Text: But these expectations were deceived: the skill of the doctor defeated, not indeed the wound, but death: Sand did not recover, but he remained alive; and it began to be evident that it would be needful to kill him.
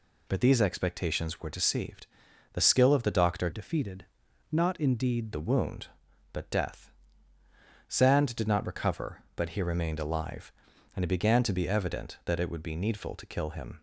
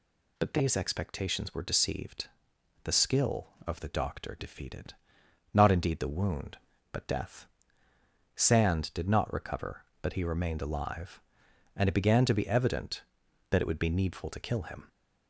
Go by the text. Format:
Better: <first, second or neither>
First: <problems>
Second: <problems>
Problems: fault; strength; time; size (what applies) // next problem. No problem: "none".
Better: second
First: changes voice from "defeated" to "indeed"; from 3.5 to 5.3 s; 1.8 s long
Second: none